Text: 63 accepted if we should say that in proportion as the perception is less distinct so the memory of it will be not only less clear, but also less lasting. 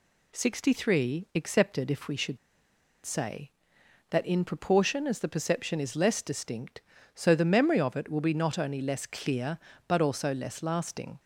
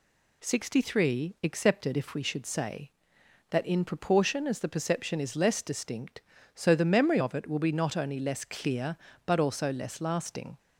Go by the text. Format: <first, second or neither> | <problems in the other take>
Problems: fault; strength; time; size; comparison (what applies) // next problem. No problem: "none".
second | pauses between "should" and "say"; noticeable; at 2.3 s; 0.67 s long